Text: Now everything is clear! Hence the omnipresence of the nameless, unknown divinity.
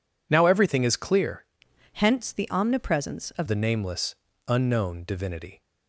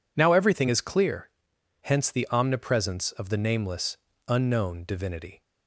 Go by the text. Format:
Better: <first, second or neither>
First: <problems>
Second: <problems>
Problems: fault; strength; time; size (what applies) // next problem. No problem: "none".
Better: second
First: changes voice from "Hence" to "of"; from 1.9 to 3.4 s; 1.5 s long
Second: none